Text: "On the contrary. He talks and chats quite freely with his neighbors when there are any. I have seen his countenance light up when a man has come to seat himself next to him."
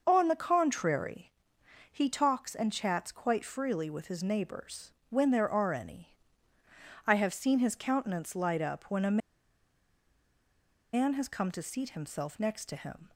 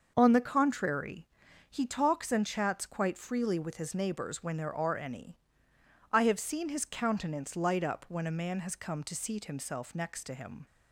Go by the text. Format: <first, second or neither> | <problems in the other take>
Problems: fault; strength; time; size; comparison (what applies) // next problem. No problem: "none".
second | starts louder than the rest; until 1.0 s; 6 dB; also in the second // pauses between "neighbors" and "when"; slight; at 4.9 s; 0.16 s long // pauses between "a" and "man"; strong; at 9.1 s; 1.7 s long